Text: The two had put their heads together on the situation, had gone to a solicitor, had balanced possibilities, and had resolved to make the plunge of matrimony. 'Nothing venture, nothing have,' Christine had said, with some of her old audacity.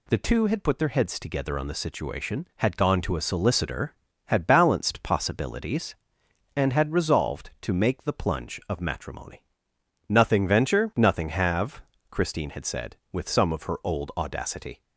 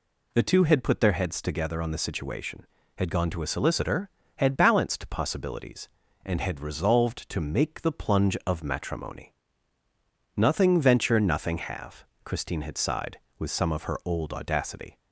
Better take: first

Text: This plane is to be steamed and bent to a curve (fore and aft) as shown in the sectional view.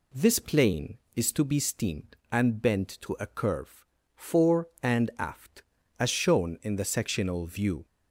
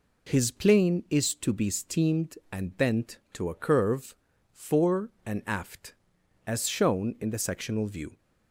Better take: first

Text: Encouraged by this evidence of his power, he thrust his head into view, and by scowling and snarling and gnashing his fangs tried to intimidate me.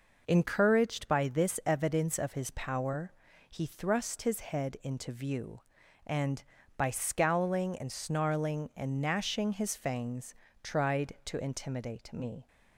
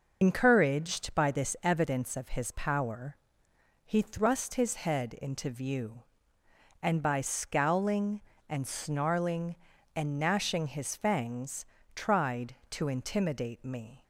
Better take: first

